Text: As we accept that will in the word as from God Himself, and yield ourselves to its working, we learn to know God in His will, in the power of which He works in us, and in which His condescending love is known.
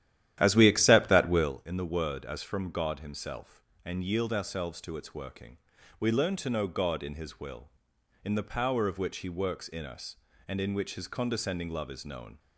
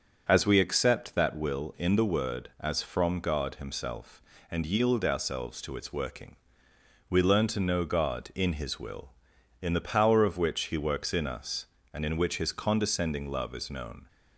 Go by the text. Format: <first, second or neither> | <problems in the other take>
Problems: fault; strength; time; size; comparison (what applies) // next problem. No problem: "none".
second | starts louder than the rest; strong; until 1.6 s; 12 dB